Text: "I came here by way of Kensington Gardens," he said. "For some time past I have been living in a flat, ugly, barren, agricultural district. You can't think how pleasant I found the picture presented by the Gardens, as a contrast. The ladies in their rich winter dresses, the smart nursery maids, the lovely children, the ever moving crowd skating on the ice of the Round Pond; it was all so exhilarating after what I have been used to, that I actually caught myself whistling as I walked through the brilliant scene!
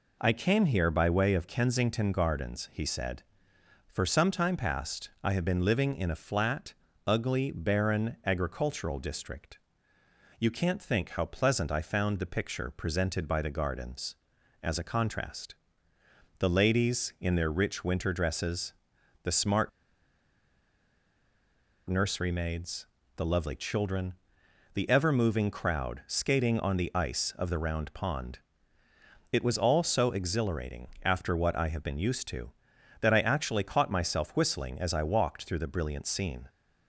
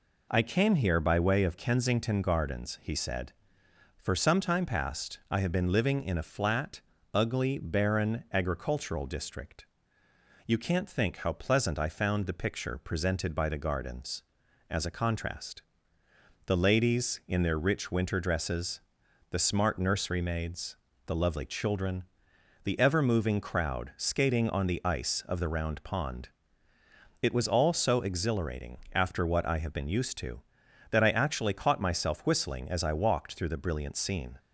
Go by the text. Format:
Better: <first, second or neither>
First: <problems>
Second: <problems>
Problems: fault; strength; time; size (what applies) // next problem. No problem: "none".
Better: second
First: pauses between "smart" and "nursery"; strong; at 19.6 s; 2.1 s long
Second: none